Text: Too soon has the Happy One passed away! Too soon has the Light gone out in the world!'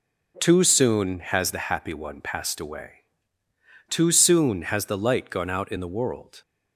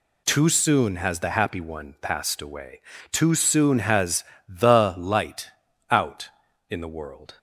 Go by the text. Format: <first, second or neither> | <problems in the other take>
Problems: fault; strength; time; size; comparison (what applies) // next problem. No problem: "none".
first | pauses between "has" and "the"; slight; at 4.2 s; 0.24 s long // skips "gone"; at 5.6 s